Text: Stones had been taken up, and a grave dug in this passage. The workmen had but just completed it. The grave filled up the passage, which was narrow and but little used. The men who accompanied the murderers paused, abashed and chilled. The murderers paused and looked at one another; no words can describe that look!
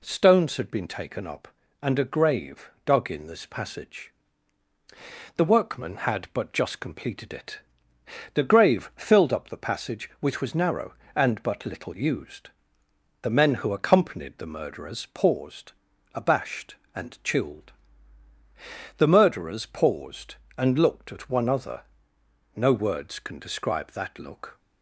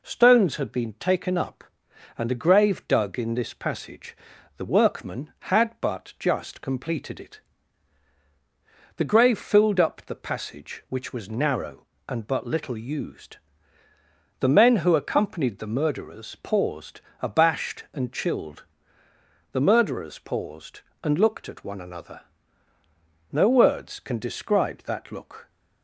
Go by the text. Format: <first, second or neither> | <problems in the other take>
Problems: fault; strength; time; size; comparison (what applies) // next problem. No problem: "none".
second | says "other" for "another"; at 21.4 s